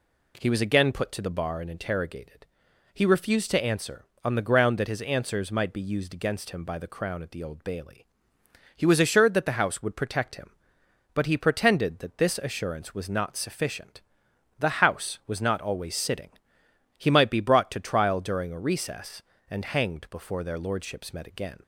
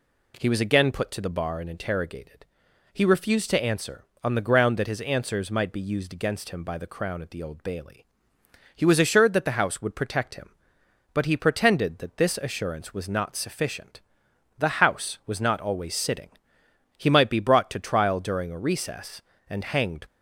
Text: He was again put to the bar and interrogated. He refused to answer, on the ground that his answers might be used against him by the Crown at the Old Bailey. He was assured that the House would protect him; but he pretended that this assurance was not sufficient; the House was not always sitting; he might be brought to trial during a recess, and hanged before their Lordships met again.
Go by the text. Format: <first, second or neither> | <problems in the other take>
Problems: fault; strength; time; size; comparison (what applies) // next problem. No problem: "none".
first | stops before "before their Lordships met again"; at 20.0 s